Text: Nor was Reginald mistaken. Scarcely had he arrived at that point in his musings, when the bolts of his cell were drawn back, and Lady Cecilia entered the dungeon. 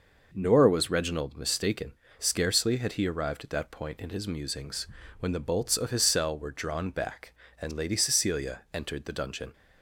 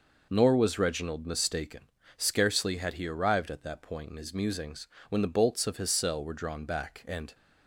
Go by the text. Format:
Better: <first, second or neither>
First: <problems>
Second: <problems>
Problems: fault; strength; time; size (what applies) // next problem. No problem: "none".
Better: first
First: none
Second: stops before "Lady Cecilia entered the dungeon"; at 7.3 s